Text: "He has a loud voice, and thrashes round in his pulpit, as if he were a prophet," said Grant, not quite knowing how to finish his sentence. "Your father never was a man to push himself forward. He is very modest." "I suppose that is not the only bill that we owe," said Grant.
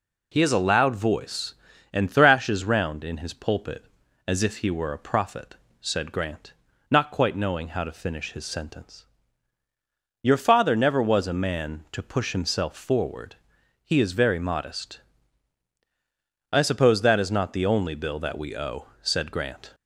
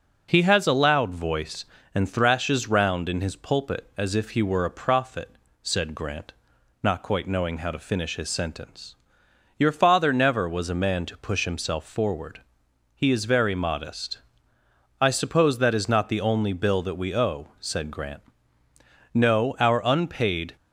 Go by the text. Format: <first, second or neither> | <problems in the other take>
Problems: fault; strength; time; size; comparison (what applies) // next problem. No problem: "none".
first | goes on to say "No our unpaid"; from 19.1 s on; 1.4 s long